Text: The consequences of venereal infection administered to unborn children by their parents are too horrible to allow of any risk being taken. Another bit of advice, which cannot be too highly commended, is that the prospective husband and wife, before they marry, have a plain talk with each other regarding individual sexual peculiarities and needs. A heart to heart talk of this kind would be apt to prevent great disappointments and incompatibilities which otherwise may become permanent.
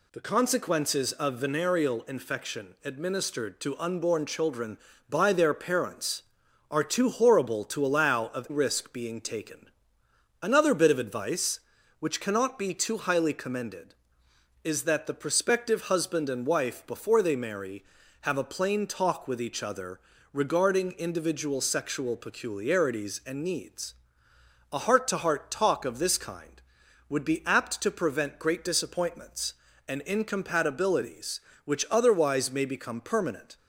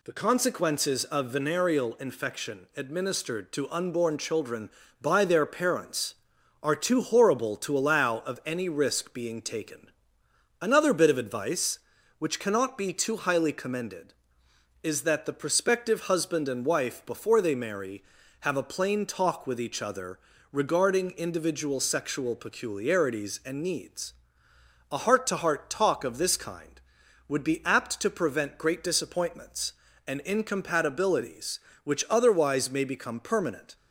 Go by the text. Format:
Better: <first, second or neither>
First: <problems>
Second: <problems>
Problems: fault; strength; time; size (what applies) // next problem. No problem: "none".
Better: second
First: skips "any"; at 8.4 s // pauses between "other" and "regarding"; slight; at 19.9 s; 0.36 s long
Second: pauses between "other" and "regarding"; slight; at 20.1 s; 0.36 s long